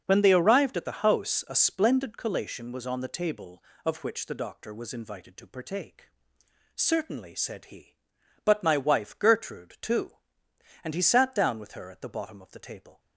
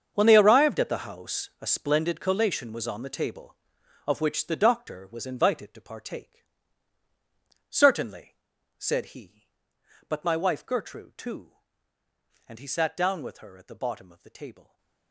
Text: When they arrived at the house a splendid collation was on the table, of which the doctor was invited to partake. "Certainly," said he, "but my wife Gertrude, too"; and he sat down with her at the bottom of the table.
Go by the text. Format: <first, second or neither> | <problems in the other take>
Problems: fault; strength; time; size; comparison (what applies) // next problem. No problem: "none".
first | gets quieter; strong; throughout; 16.5 dB // starts louder than the rest; strong; until 1.1 s; 7 dB; also in the first